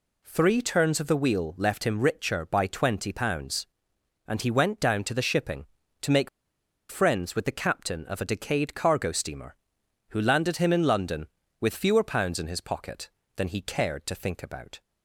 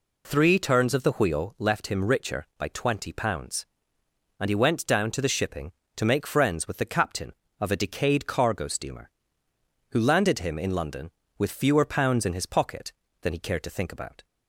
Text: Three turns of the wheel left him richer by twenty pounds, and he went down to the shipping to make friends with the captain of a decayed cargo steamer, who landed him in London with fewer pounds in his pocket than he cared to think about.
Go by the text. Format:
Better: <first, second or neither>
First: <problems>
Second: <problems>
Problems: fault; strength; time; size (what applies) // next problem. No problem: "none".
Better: second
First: pauses between "make" and "friends"; noticeable; at 6.2 s; 0.61 s long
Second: none